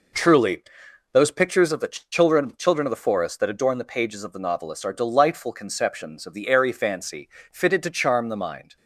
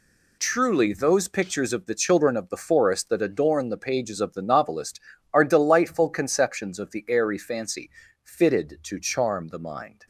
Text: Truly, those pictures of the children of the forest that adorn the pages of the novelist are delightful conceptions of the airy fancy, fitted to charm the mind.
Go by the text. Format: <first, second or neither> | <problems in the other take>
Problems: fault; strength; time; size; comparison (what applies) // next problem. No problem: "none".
second | says "children" twice; at 2.5 s